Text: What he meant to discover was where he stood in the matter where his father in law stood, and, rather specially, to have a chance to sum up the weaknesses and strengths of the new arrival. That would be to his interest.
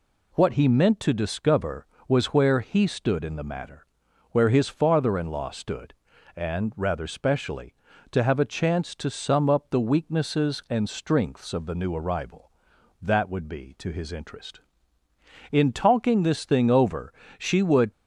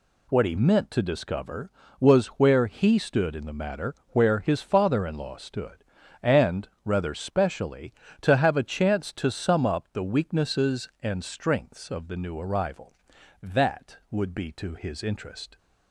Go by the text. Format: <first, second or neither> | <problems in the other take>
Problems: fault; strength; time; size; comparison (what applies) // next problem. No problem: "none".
second | pauses between "matter" and "where"; noticeable; at 3.8 s; 0.46 s long; slight in the second // goes on to say "In talking this thing over she would"; strong; from 15.4 s on; 2.4 s long